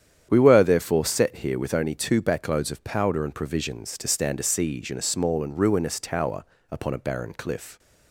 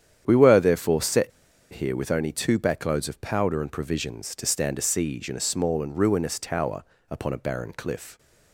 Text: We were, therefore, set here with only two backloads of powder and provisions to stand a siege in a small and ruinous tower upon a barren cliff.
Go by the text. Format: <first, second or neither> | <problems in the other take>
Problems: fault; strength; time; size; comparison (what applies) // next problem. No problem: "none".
first | starts louder than the rest; strong; until 1.2 s; 9 dB; strong in the first // pauses between "set" and "here"; at 1.3 s; 0.43 s long // pauses between "tower" and "upon"; slight; at 6.8 s; 0.26 s long; slight in the first